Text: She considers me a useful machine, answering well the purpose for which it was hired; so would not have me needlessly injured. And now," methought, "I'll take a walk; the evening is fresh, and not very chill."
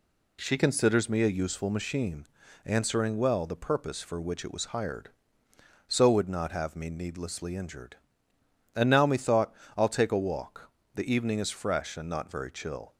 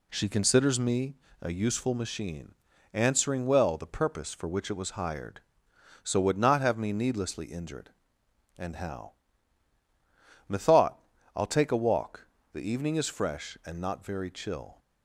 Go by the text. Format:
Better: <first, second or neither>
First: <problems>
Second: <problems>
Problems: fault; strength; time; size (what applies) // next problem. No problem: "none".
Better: first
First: none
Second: pauses between "me" and "a"; slight; at 1.1 s; 0.26 s long // says "how" for "now"; at 8.7 s